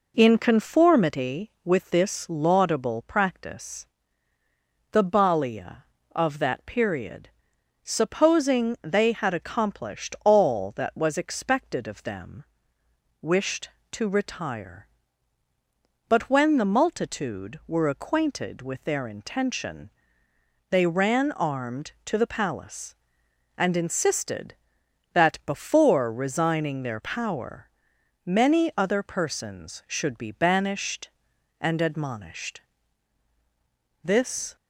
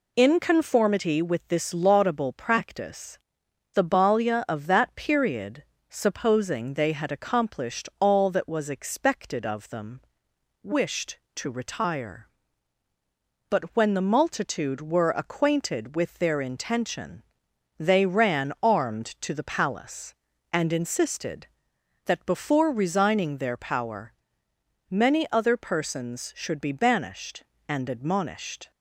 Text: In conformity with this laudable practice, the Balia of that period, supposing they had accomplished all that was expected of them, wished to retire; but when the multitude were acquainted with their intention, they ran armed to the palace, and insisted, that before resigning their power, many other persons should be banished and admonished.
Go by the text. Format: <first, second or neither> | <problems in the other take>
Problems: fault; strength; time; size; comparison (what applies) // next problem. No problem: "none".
second | goes on to say "This"; from 34.0 s on; 0.52 s long